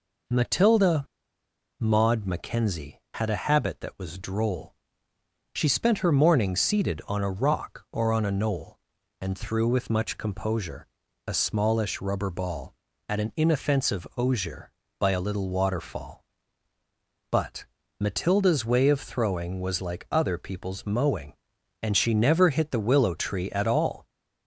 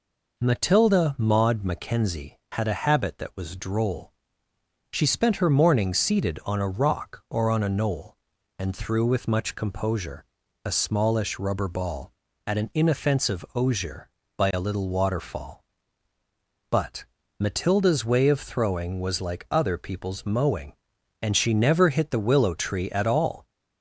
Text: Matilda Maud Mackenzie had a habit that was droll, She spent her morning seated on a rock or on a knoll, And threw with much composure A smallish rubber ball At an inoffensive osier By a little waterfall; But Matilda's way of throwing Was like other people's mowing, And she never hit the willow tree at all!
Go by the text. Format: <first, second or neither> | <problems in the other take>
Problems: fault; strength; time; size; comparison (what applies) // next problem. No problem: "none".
second | pauses between "Matilda" and "Maud"; noticeable; at 1.0 s; 0.75 s long // pauses between "composure" and "A"; at 10.8 s; 0.38 s long; also in the second // pauses between "But" and "Matilda's"; at 17.6 s; 0.38 s long; also in the second